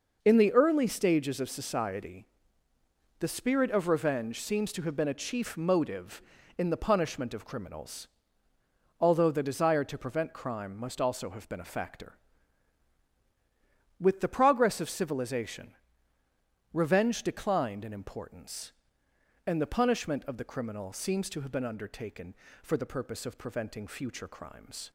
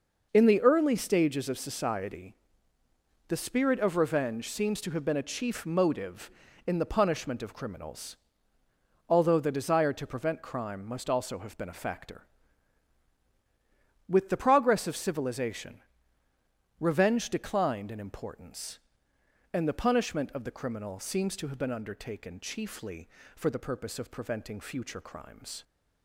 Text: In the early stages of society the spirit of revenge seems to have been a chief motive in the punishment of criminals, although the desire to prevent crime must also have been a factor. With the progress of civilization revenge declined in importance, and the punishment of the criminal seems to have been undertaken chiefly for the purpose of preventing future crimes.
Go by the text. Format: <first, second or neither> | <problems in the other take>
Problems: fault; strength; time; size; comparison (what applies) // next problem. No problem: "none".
second | pauses between "society" and "the"; noticeable; at 2.2 s; 0.94 s long; noticeable in the second // pauses between "civilization" and "revenge"; at 15.7 s; 1.0 s long; also in the second // skips "chiefly"; at 22.4 s